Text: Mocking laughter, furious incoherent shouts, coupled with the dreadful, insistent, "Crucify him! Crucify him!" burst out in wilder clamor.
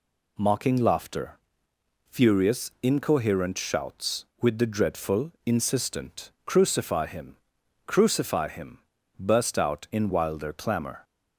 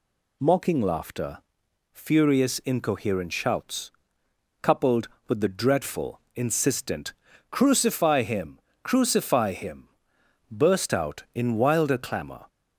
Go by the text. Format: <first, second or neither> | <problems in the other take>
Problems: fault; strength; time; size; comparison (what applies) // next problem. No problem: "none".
second | skips "coupled"; at 4.3 s